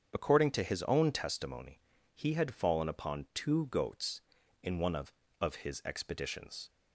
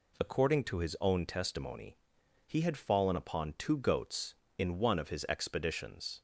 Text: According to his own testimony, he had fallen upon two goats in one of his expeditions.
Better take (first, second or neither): second